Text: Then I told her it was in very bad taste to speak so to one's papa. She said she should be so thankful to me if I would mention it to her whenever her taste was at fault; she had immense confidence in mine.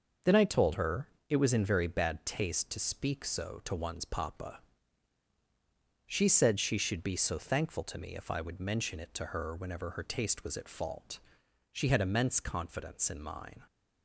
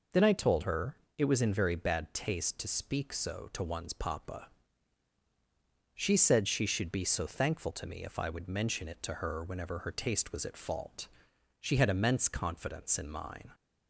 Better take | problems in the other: second | gets quieter; throughout; 6.5 dB // pauses between "her" and "it"; slight; at 1.0 s; 0.22 s long; slight in the second

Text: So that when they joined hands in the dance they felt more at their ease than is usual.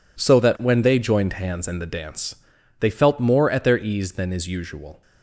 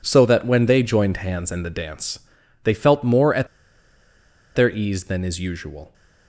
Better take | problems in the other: first | pauses between "dance" and "they"; noticeable; at 2.1 s; 0.46 s long; noticeable in the first // pauses between "at" and "their"; at 3.4 s; 1.0 s long

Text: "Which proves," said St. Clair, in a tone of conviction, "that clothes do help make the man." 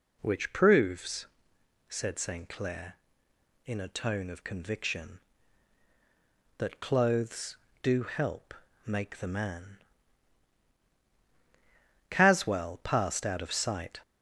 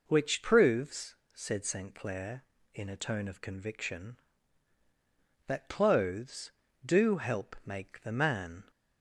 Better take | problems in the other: second | pauses between "help" and "make"; slight; at 8.5 s; 0.32 s long // goes on to say "Caswell passed out of sight"; strong; from 12.0 s on; 1.9 s long

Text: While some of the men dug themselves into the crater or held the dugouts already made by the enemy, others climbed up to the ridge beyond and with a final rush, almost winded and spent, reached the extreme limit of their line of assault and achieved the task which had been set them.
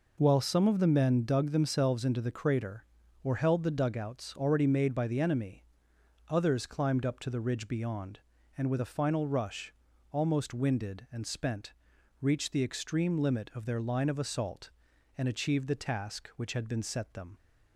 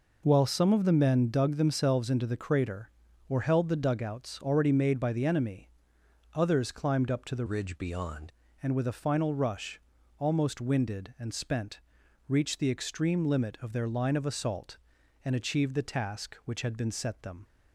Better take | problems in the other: first | changes voice from "ridge" to "beyond"; from 7.4 to 8.3 s; 0.9 s long

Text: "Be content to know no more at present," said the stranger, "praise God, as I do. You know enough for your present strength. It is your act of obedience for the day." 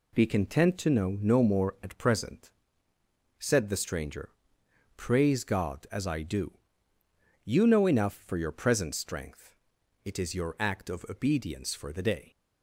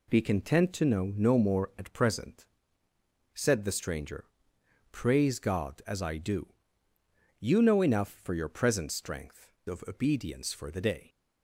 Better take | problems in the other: first | skips "It is your act"; at 9.5 s

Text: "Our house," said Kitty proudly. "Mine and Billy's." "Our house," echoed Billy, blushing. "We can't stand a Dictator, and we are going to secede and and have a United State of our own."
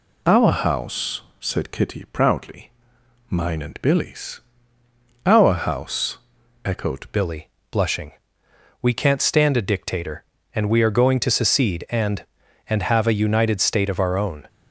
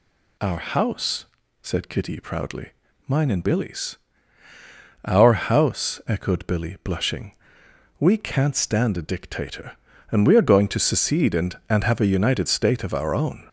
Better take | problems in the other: second | changes voice at "Billy"; from 7.1 s on; 7.3 s long

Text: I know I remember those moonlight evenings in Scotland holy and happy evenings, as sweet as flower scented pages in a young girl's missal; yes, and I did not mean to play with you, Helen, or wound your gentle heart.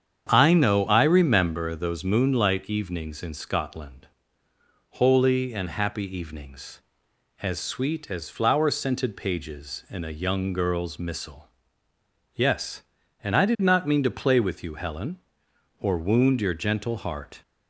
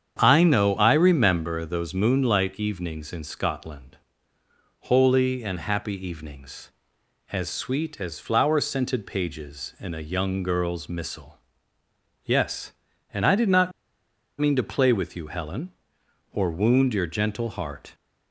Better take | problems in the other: first | starts louder than the rest; strong; until 1.2 s; 8 dB; strong in the first // pauses between "Scotland" and "holy"; noticeable; at 3.9 s; 0.84 s long; noticeable in the first // pauses between "not" and "mean"; noticeable; at 13.7 s; 0.68 s long

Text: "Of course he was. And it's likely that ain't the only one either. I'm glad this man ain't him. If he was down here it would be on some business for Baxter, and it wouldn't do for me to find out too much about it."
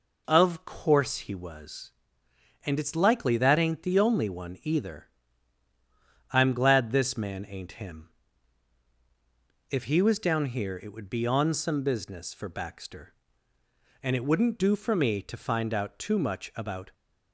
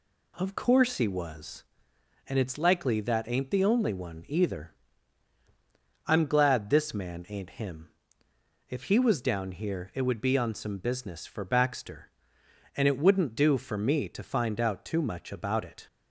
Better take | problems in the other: second | stops before "it"; at 16.9 s

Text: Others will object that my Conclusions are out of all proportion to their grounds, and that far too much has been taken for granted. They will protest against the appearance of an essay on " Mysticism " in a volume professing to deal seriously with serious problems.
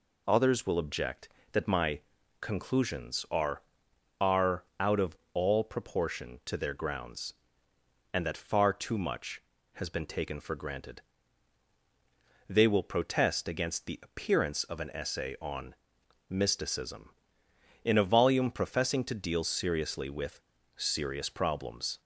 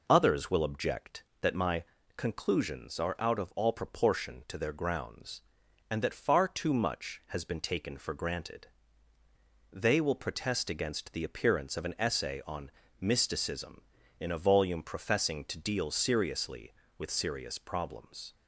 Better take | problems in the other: second | pauses between "my" and "Conclusions"; at 2.0 s; 0.40 s long; slight in the second // says "are" twice; at 4.2 s // pauses between "of" and "all"; slight; at 5.1 s; 0.16 s long // pauses between "with" and "serious"; slight; at 20.4 s; 0.34 s long

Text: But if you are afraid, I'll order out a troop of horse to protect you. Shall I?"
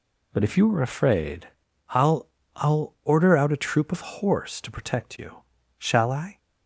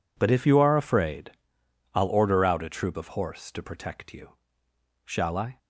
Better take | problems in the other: second | says "I'll" twice; at 2.5 s

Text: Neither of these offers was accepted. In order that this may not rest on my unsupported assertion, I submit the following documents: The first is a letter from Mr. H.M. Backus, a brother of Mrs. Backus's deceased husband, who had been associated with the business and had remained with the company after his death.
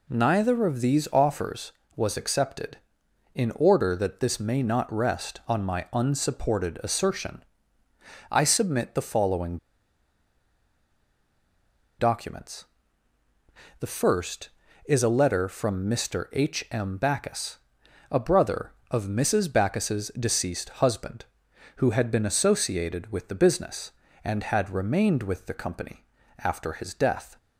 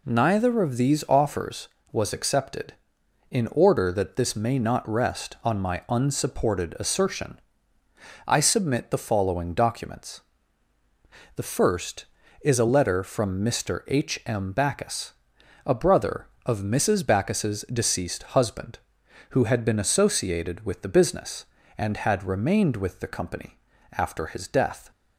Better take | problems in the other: second | pauses between "following" and "documents"; strong; at 9.5 s; 2.4 s long // pauses between "company" and "after"; slight; at 26.0 s; 0.34 s long; slight in the second

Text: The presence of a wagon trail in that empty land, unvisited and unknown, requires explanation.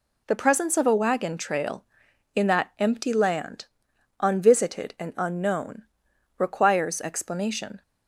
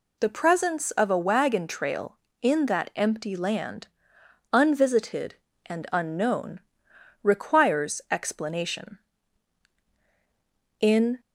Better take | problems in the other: first | goes on to say "In"; slight; from 10.7 s on; 0.40 s long

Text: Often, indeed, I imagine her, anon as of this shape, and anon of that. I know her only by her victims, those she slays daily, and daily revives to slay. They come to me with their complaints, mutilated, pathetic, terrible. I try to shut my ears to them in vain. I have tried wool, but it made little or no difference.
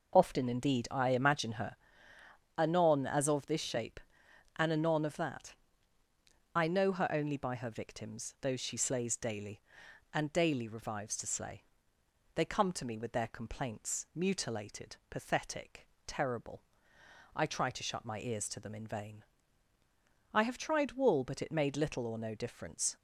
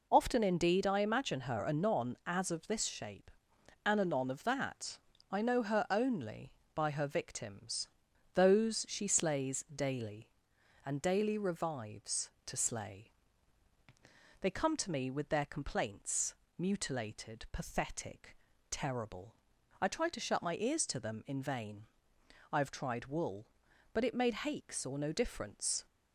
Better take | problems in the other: first | says "hakes" for "little"; at 24.3 s

